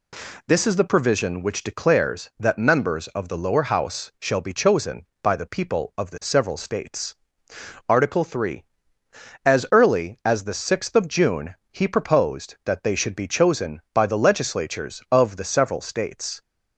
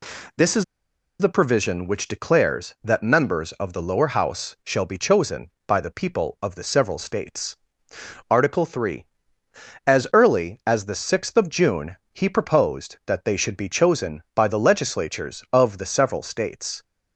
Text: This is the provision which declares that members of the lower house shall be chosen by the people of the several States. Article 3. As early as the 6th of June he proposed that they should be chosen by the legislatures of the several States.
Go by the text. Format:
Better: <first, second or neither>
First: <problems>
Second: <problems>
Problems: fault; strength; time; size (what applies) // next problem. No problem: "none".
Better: first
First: pauses between "June" and "he"; slight; at 11.5 s; 0.18 s long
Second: pauses between "is" and "the"; noticeable; at 0.6 s; 0.55 s long // pauses between "June" and "he"; slight; at 11.9 s; 0.18 s long